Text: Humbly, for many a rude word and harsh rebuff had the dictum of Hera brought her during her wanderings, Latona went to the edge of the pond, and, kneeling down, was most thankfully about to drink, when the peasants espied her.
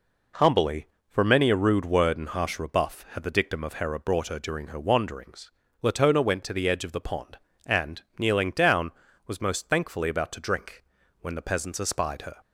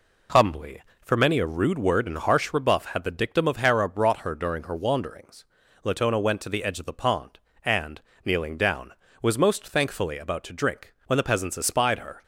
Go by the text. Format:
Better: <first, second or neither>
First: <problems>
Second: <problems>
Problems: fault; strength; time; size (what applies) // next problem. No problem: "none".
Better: neither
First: none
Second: none